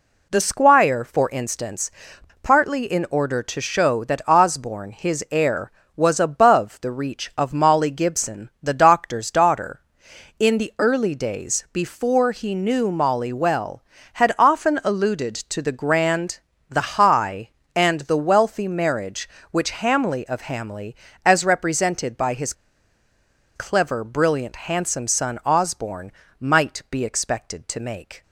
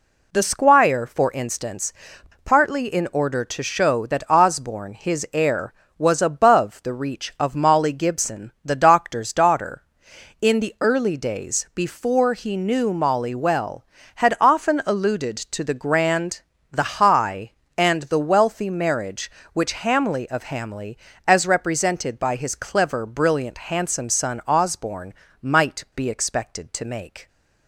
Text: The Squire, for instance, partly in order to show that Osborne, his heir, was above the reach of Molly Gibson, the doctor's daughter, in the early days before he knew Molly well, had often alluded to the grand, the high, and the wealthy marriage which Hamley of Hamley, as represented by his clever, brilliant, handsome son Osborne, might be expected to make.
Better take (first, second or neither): second